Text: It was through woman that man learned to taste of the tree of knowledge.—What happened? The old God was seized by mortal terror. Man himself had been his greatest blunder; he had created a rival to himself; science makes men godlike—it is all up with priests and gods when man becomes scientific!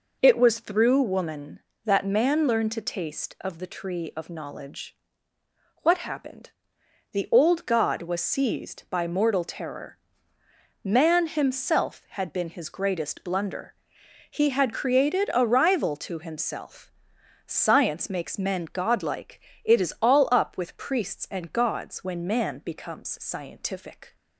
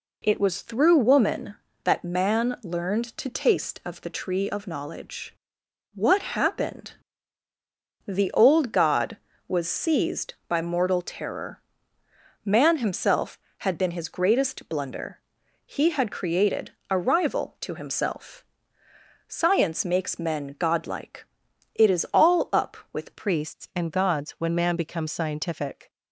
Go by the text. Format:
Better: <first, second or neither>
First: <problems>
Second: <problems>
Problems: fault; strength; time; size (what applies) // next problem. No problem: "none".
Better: first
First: none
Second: pauses between "created" and "a"; slight; at 16.7 s; 0.18 s long // changes voice at "priests"; from 23.1 s on; 2.7 s long